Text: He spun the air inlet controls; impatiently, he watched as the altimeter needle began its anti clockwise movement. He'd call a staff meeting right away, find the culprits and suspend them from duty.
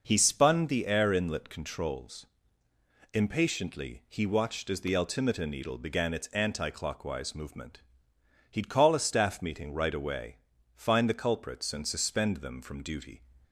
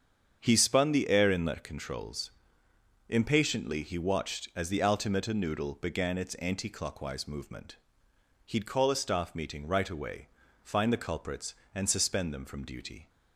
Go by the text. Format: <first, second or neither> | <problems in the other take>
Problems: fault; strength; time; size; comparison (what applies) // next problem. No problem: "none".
first | starts louder than the rest; strong; until 1.4 s; 7.5 dB // says "noodle" for "needle"; at 5.3 s